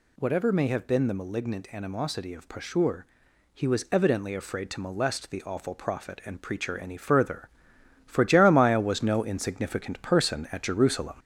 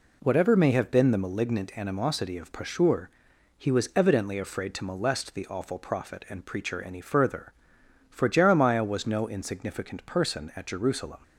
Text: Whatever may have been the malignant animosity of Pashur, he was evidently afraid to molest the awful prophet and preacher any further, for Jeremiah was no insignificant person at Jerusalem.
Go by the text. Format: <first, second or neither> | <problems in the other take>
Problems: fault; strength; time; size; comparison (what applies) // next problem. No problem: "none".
second | gets louder; slight; throughout; 3 dB